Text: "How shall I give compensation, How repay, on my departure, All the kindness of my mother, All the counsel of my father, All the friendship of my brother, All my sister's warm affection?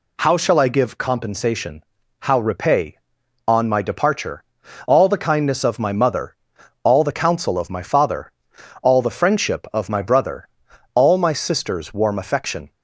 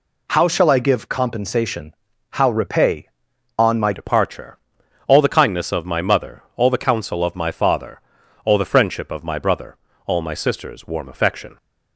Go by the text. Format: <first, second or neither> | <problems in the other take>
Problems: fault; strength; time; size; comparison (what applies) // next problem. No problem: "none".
first | changes voice at "departure"; from 3.9 s on; 7.6 s long